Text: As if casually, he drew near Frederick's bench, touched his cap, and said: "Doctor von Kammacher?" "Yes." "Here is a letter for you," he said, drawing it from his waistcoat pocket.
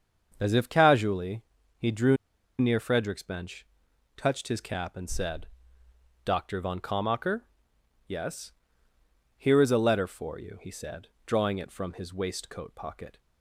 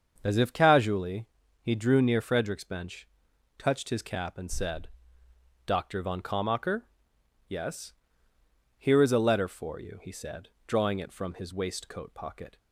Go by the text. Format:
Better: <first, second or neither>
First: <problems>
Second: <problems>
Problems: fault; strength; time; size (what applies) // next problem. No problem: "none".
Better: second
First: starts louder than the rest; until 1.3 s; 7 dB // pauses between "drew" and "near"; at 2.1 s; 0.42 s long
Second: starts louder than the rest; until 1.2 s; 7 dB